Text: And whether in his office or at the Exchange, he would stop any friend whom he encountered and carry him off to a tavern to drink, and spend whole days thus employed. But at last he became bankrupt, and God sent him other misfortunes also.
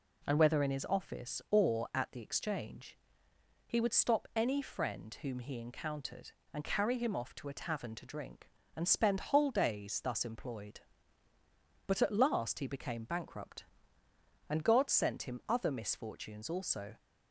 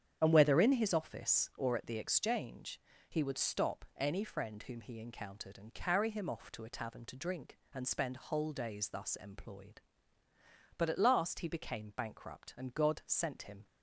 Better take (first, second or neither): first